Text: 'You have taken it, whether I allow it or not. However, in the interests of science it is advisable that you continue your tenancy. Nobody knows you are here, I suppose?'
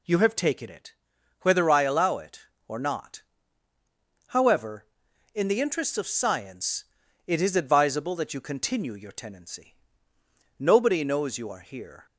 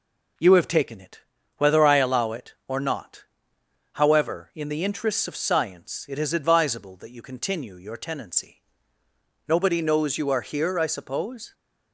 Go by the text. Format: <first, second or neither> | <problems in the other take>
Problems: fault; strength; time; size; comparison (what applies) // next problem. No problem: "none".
second | pauses between "science" and "it"; at 6.8 s; 0.42 s long // stops before "I suppose"; at 12.0 s